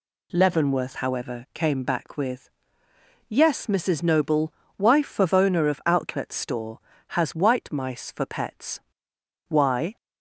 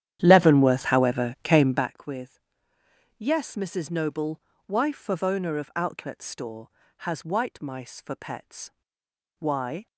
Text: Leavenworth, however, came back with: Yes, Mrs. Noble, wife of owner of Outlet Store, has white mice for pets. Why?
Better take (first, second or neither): first